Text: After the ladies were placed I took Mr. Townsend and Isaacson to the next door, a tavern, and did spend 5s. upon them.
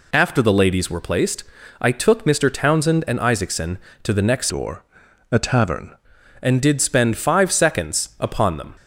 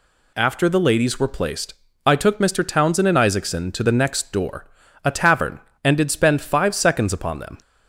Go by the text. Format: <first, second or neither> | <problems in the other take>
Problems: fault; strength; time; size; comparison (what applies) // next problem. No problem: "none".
second | pauses between "placed" and "I"; at 1.4 s; 0.38 s long; slight in the second // changes voice from "door" to "tavern"; from 4.4 to 5.9 s; 1.5 s long